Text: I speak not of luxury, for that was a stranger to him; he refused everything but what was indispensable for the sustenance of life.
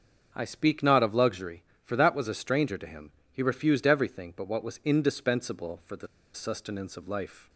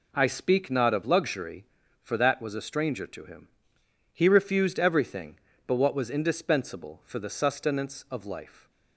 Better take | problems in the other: second | starts louder than the rest; until 1.3 s; 6.5 dB // pauses between "the" and "sustenance"; slight; at 6.0 s; 0.28 s long

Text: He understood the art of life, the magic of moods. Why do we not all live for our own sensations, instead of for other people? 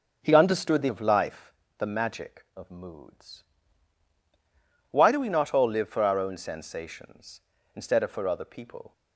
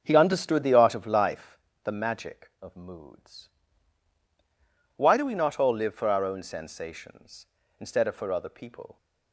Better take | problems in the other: second | starts louder than the rest; until 1.2 s; 7 dB; also in the second // skips "art"; at 0.8 s

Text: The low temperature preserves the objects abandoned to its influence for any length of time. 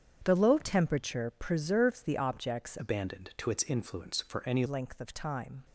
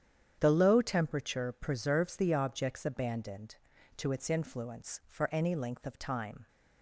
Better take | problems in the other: second | starts louder than the rest; strong; until 1.2 s; 8 dB; strong in the second // changes voice from "abandoned" to "any"; from 2.7 to 4.6 s; 1.9 s long

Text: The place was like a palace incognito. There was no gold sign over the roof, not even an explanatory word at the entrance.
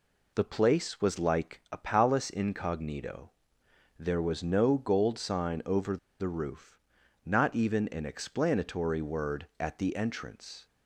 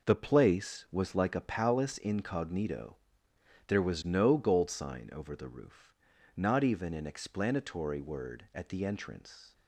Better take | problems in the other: second | pauses between "over" and "the"; slight; at 5.9 s; 0.22 s long

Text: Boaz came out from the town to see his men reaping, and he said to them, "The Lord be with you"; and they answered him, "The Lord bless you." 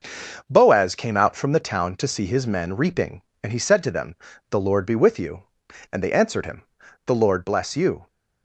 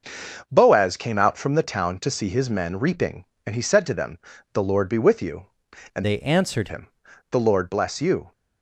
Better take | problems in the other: first | changes voice from "they" to "answered"; from 6.0 to 6.6 s; 0.6 s long

